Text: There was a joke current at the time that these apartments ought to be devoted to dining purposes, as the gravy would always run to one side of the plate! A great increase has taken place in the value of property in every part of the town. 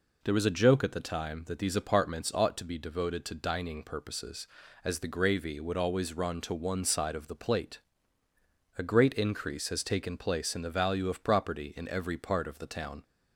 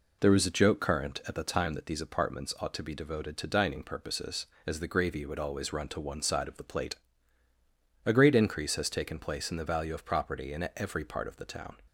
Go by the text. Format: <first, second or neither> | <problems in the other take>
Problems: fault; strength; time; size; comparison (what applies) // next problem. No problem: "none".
second | skips "current"; at 0.8 s